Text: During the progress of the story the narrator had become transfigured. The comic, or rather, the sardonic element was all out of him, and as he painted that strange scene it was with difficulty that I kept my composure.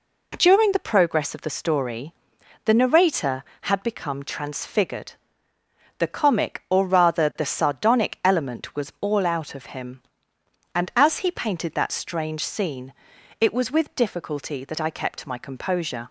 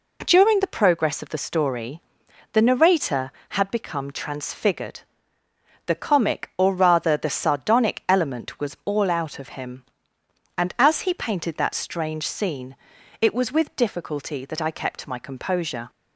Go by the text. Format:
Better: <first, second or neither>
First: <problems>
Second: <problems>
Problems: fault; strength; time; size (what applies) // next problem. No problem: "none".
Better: neither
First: pauses between "story" and "the"; noticeable; at 2.1 s; 0.52 s long // pauses between "scene" and "it"; noticeable; at 12.9 s; 0.48 s long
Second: pauses between "story" and "the"; noticeable; at 1.9 s; 0.52 s long // pauses between "scene" and "it"; noticeable; at 12.7 s; 0.46 s long